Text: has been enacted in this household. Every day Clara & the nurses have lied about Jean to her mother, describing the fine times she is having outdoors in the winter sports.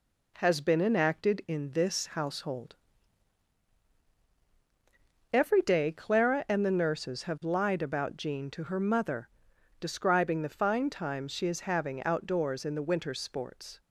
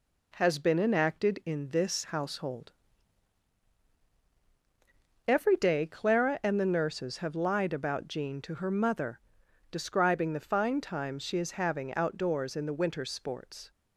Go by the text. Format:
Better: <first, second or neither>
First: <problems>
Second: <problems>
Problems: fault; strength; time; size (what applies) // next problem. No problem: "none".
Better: neither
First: none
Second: none